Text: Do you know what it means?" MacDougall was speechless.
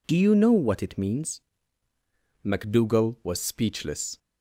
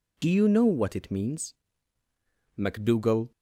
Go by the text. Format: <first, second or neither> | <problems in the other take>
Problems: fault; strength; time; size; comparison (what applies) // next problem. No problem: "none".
first | stops before "was speechless"; at 3.3 s